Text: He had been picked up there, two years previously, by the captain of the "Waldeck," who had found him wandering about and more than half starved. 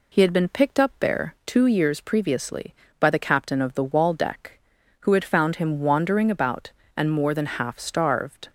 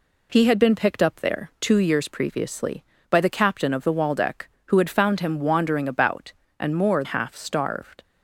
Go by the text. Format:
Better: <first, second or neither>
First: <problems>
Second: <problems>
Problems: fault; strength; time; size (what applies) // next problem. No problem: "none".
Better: first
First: none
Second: skips "than"; at 7.0 s